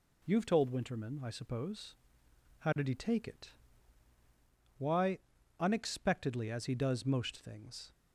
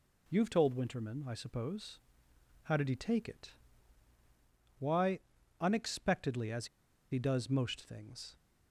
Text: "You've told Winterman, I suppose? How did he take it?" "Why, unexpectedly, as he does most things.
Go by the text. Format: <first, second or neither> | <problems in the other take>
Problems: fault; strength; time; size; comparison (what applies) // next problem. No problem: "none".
first | pauses between "as" and "he"; at 6.6 s; 0.45 s long